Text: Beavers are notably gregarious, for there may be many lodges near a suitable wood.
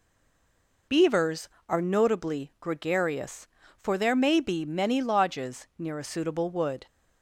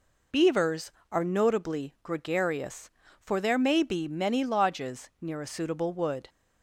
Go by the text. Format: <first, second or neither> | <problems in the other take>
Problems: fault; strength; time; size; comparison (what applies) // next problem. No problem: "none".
second | stays silent before the first word; slight; until 0.8 s; 0.8 s long